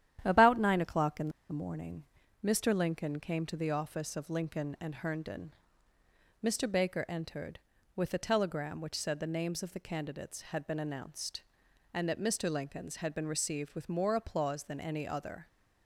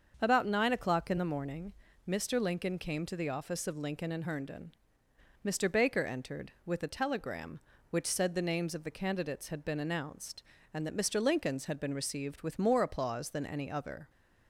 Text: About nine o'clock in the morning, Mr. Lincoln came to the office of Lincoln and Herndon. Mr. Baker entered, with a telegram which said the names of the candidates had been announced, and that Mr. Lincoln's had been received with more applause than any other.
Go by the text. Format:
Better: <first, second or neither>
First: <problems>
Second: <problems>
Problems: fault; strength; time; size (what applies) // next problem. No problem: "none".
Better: second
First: starts louder than the rest; strong; until 1.2 s; 11 dB // pauses between "in" and "the"; slight; at 1.2 s; 0.19 s long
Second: starts louder than the rest; until 1.2 s; 6.5 dB